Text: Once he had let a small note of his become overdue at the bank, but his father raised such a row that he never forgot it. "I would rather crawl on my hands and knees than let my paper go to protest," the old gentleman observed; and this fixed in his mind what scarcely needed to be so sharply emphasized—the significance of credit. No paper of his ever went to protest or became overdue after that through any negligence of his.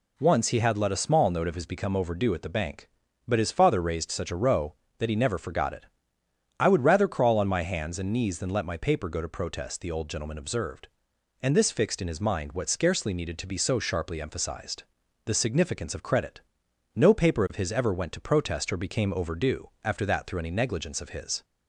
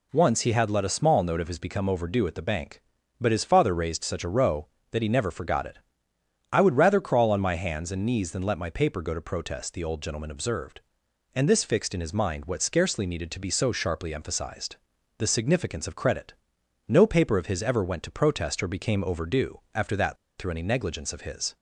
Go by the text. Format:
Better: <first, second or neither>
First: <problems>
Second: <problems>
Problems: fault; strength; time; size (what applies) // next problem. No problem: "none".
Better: first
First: pauses between "overdue" and "after"; slight; at 19.6 s; 0.16 s long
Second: pauses between "overdue" and "after"; slight; at 19.5 s; 0.16 s long // pauses between "that" and "through"; slight; at 20.1 s; 0.22 s long